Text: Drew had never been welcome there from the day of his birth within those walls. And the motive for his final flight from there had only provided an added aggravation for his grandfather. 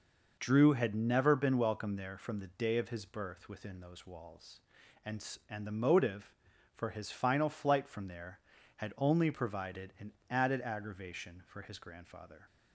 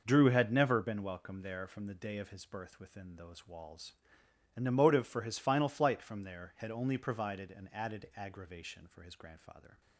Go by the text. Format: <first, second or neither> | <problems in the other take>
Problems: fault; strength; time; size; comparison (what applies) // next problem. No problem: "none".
second | says "And" twice; at 5.4 s // pauses between "an" and "added"; slight; at 10.1 s; 0.18 s long